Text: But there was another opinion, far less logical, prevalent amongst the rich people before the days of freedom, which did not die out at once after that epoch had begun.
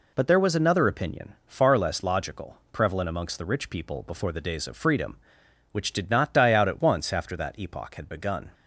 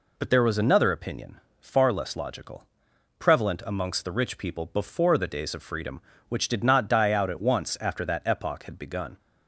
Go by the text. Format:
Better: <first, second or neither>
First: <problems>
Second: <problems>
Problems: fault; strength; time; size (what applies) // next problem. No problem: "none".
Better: neither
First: none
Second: none